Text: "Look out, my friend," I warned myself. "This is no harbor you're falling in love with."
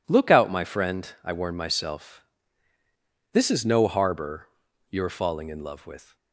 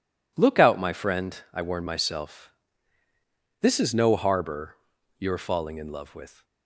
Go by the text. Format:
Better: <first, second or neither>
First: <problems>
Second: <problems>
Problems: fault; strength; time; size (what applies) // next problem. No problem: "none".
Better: neither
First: pauses between "harbor" and "you're"; at 4.4 s; 0.42 s long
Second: pauses between "harbor" and "you're"; at 4.7 s; 0.42 s long